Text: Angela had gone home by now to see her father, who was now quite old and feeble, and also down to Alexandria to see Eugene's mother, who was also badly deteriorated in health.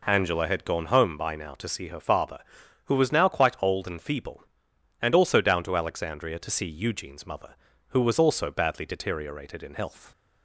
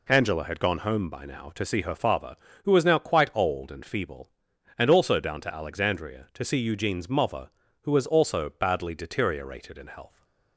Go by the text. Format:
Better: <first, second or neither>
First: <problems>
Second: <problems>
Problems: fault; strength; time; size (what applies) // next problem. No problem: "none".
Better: neither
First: none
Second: none